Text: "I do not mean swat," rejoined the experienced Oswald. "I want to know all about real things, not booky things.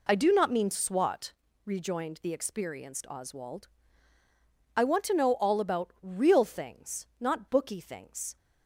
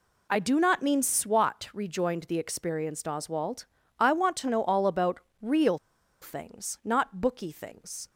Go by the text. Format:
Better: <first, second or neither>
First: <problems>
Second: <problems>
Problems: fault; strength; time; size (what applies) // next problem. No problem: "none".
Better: first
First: none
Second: pauses between "about" and "real"; slight; at 5.2 s; 0.22 s long // pauses between "real" and "things"; at 5.7 s; 0.45 s long